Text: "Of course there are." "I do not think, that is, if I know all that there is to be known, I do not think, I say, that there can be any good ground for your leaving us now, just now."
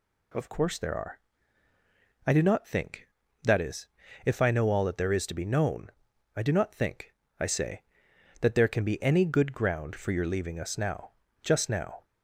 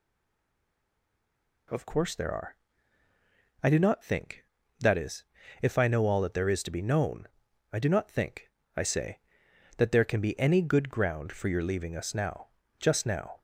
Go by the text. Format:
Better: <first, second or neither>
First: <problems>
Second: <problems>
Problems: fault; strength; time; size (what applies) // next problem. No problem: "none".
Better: first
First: none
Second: stays silent before the first word; noticeable; until 1.6 s; 1.6 s long